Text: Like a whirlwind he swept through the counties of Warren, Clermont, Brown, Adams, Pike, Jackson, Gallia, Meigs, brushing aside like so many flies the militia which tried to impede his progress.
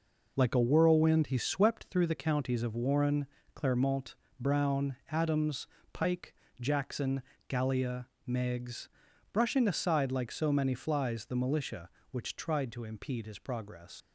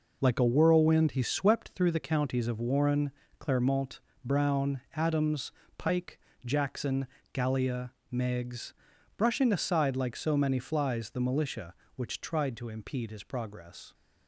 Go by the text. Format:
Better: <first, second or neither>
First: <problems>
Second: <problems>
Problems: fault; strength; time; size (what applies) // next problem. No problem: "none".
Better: second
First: leaves "progress" unfinished; at 14.0 s; 85 ms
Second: none